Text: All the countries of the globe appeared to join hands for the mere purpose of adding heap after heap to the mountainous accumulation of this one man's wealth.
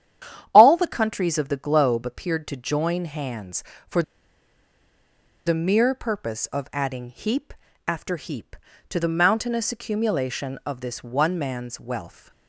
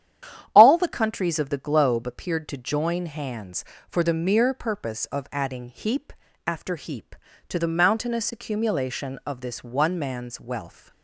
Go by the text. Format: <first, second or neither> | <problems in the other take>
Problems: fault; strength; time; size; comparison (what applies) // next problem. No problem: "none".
second | starts louder than the rest; strong; until 1.5 s; 10 dB; strong in the second // pauses between "for" and "the"; strong; at 4.0 s; 1.4 s long // pauses between "heap" and "after"; slight; at 7.5 s; 0.34 s long; slight in the second